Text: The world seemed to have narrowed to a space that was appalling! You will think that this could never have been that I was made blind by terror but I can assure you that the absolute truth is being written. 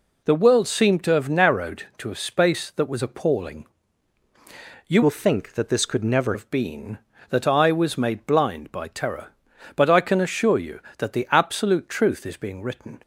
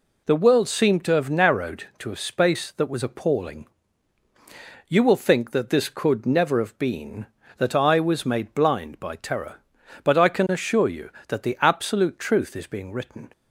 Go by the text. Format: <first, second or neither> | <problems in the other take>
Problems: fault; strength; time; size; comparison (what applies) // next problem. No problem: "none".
second | changes voice from "will" to "never"; from 5.0 to 6.3 s; 1.3 s long